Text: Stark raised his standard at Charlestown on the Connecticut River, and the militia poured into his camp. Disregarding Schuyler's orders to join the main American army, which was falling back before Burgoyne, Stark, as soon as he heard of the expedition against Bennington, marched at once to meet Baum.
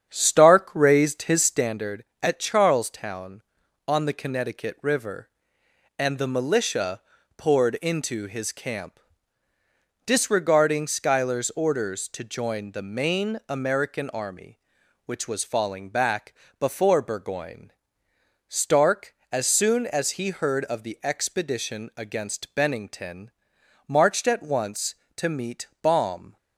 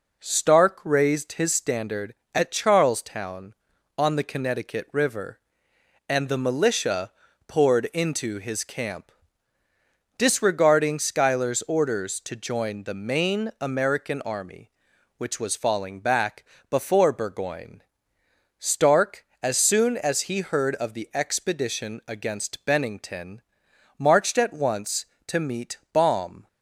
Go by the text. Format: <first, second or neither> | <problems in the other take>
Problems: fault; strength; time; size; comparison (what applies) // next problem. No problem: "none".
second | starts louder than the rest; strong; until 1.8 s; 8.5 dB // pauses between "militia" and "poured"; slight; at 6.9 s; 0.36 s long; slight in the second // pauses between "back" and "before"; slight; at 16.3 s; 0.24 s long; slight in the second